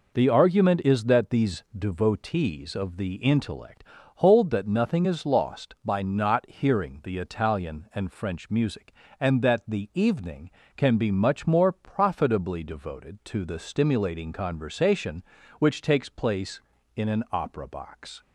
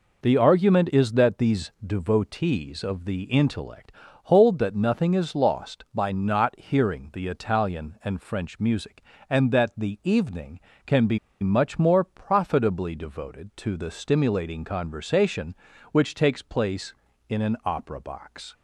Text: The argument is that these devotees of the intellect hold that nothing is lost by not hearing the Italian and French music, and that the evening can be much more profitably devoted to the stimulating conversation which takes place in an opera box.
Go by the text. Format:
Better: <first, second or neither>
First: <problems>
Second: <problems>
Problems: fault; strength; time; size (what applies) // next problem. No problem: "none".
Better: first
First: pauses between "intellect" and "hold"; slight; at 3.8 s; 0.34 s long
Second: pauses between "intellect" and "hold"; slight; at 3.9 s; 0.34 s long // pauses between "be" and "much"; slight; at 11.1 s; 0.24 s long